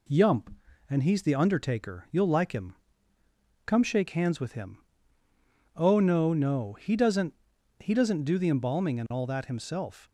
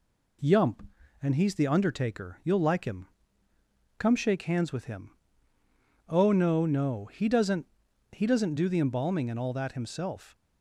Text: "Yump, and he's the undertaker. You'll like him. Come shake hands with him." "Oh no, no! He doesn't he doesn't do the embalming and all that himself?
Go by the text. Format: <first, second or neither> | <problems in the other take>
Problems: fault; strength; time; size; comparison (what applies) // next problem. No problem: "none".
neither | pauses between "doesn't" and "he"; noticeable; the same in both